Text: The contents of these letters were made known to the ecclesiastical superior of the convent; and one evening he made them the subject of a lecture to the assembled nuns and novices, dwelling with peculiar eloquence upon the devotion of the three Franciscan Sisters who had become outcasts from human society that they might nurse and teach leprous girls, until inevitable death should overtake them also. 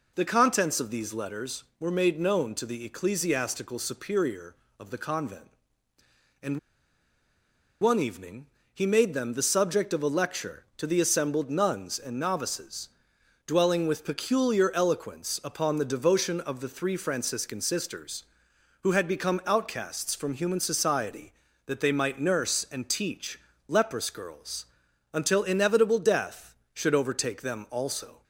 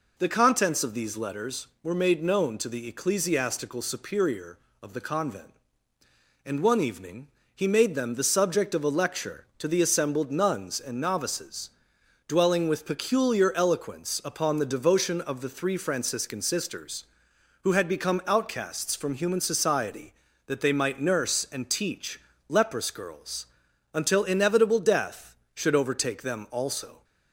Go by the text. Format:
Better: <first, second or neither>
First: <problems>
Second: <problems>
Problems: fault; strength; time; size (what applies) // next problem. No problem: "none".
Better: second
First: pauses between "and" and "one"; at 6.5 s; 1.2 s long // pauses between "evening" and "he"; slight; at 8.4 s; 0.26 s long // pauses between "teach" and "leprous"; slight; at 23.3 s; 0.28 s long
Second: pauses between "evening" and "he"; slight; at 7.2 s; 0.26 s long // pauses between "teach" and "leprous"; slight; at 22.1 s; 0.28 s long